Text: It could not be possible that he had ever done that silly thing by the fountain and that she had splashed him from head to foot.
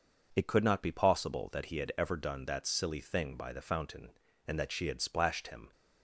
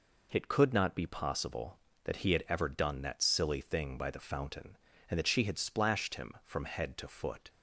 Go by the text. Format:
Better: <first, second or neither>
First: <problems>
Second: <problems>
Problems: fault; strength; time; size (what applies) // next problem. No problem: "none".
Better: second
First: stops before "from head to foot"; at 5.7 s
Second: none